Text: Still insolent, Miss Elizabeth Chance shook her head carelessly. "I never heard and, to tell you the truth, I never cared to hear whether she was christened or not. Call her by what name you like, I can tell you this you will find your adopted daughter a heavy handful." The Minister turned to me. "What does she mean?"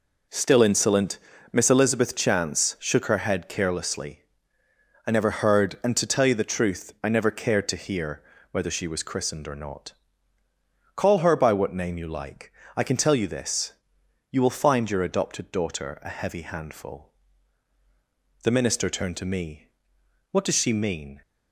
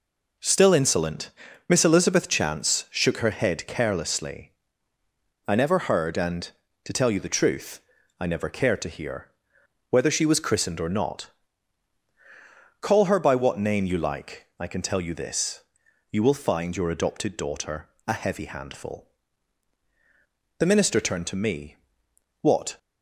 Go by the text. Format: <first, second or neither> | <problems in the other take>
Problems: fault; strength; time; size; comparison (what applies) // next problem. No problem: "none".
first | pauses between "hear" and "whether"; noticeable; at 9.3 s; 0.58 s long; slight in the first // pauses between "this" and "you"; noticeable; at 15.6 s; 0.48 s long; noticeable in the first // pauses between "daughter" and "a"; slight; at 17.8 s; 0.18 s long // stops before "does she mean"; at 22.7 s